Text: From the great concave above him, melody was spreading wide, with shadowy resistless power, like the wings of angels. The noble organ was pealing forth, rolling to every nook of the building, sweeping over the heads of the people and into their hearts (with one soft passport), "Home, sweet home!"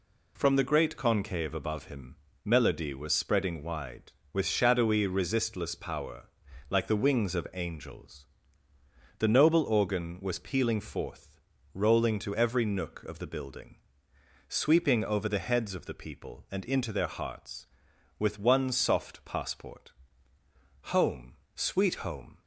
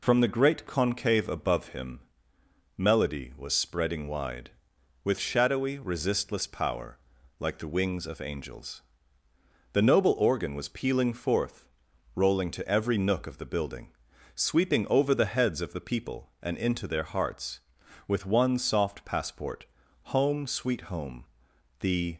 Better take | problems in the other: first | goes on to say "The"; slight; from 21.7 s on; 0.38 s long

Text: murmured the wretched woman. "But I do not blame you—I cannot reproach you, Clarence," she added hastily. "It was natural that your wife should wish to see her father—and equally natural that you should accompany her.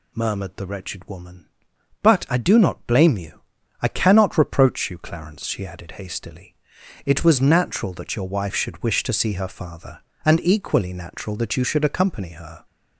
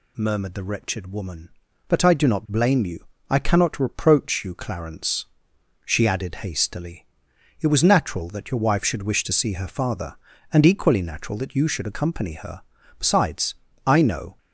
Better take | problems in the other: first | goes on to say "Besides I know"; from 12.9 s on; 1.3 s long

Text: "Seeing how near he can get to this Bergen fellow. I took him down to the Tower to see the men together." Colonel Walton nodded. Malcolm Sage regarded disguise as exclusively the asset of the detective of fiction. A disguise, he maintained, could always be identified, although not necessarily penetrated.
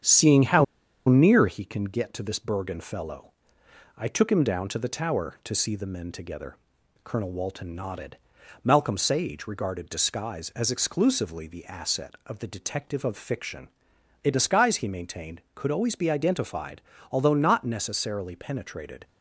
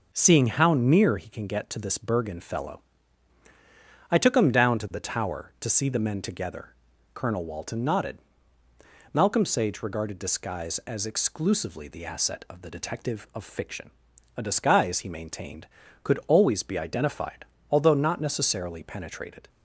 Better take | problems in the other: second | starts louder than the rest; strong; until 1.4 s; 8 dB // pauses between "how" and "near"; at 0.6 s; 0.43 s long

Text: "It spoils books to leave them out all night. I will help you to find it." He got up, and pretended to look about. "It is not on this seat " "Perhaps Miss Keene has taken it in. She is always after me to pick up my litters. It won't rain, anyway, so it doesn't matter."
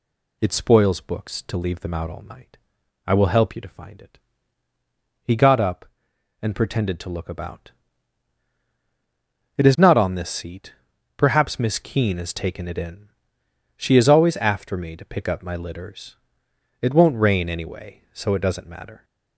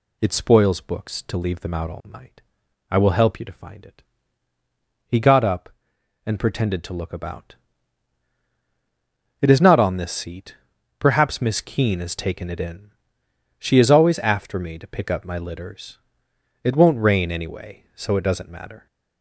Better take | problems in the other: neither | none

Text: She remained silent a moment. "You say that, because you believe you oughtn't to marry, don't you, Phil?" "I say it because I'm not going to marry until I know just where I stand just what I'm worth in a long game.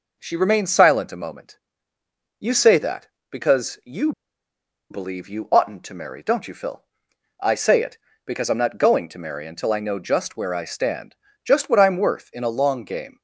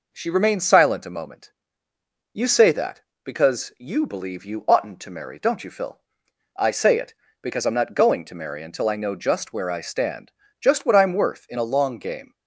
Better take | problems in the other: second | pauses between "you" and "believe"; noticeable; at 4.1 s; 0.79 s long // pauses between "stand" and "just"; slight; at 11.1 s; 0.30 s long; slight in the second

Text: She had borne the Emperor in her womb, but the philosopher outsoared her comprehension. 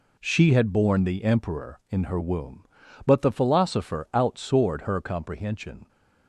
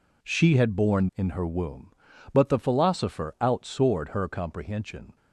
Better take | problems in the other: first | skips "the Emperor"; at 1.1 s

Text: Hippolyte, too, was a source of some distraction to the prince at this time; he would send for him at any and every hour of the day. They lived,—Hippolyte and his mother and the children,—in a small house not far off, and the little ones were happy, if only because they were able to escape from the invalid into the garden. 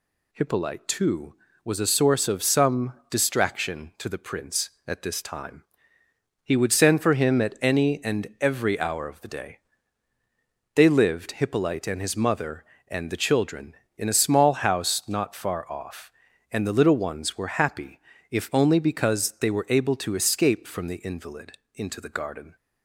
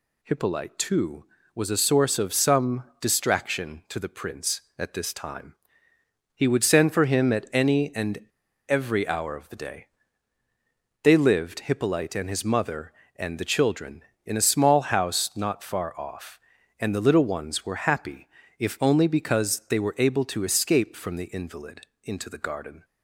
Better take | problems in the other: first | pauses between "some" and "distraction"; slight; at 2.8 s; 0.16 s long; slight in the first // pauses between "and" and "every"; at 8.2 s; 0.42 s long // pauses between "invalid" and "into"; slight; at 21.8 s; 0.20 s long; slight in the first

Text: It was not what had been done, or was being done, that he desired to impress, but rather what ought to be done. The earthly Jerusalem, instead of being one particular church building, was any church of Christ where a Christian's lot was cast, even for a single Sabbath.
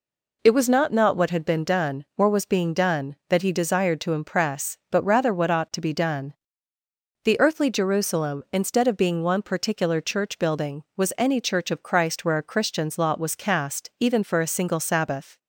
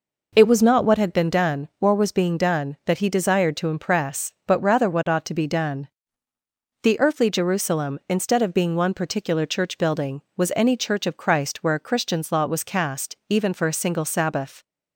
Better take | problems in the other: second | says "not" twice; at 0.9 s

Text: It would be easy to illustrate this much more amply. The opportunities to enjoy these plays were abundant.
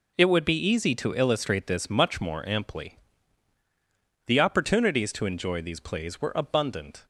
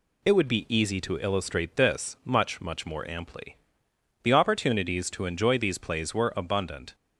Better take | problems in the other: first | says "much" twice; at 2.6 s

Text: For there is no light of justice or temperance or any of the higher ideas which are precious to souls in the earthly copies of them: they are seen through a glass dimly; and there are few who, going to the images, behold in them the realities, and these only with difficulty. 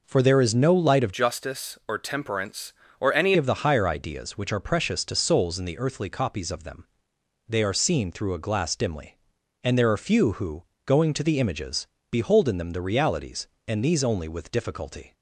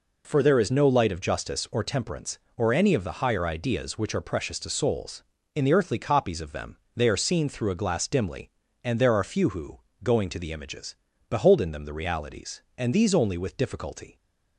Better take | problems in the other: second | changes voice from "justice" to "any"; from 1.1 to 3.3 s; 2.2 s long

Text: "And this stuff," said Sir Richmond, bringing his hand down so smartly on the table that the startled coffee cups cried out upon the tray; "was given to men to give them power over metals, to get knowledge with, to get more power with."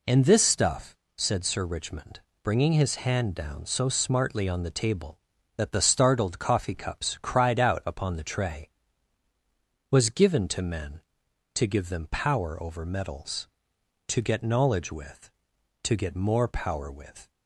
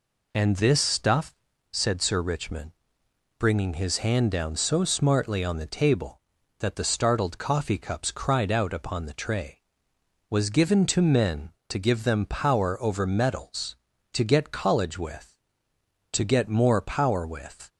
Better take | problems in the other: first | says "college" for "knowledge"; at 14.5 s

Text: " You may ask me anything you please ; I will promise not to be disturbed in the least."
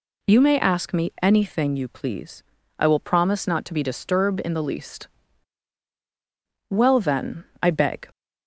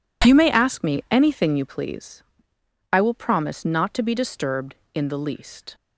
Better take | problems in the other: second | goes on to say "Well then I beg"; from 6.7 s on; 1.3 s long

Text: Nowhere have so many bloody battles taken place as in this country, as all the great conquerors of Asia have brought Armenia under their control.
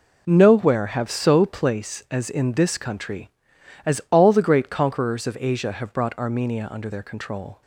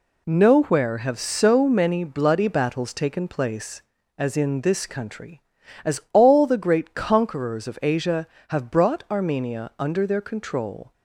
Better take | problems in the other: second | skips "many bloody battles taken"; at 1.4 s

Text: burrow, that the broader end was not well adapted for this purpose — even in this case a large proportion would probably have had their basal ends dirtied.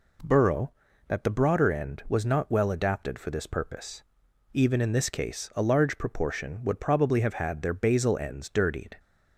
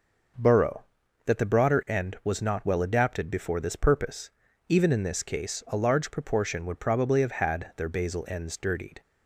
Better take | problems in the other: first | starts louder than the rest; noticeable; until 1.8 s; 6 dB // says "before" for "for"; at 3.2 s

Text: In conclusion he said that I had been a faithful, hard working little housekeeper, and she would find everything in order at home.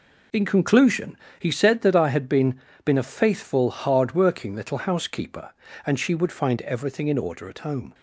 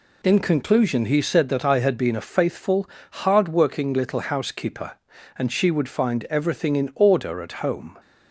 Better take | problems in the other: second | pauses between "conclusion" and "he"; slight; at 1.1 s; 0.24 s long // says "been" twice; at 2.8 s

